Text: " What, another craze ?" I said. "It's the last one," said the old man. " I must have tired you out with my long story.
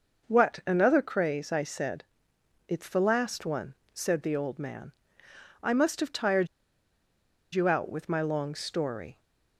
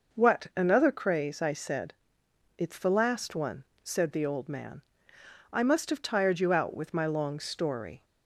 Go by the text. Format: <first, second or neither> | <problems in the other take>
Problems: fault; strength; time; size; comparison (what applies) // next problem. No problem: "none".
second | starts louder than the rest; until 1.3 s; 6.5 dB; also in the second // pauses between "tired" and "you"; at 6.4 s; 1.0 s long